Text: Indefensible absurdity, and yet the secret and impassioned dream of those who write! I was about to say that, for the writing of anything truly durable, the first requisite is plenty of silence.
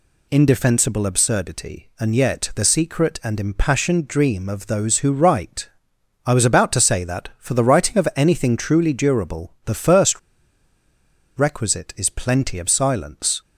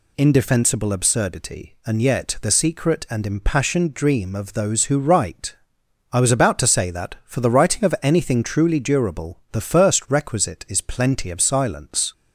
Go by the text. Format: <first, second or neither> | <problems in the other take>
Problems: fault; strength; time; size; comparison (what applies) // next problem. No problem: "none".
second | pauses between "first" and "requisite"; at 10.1 s; 1.1 s long